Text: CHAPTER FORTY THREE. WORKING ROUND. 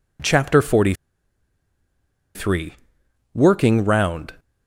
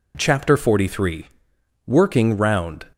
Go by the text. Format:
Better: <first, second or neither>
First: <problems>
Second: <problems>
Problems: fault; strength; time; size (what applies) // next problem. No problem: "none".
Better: second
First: pauses between "FORTY" and "THREE"; strong; at 0.9 s; 1.4 s long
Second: none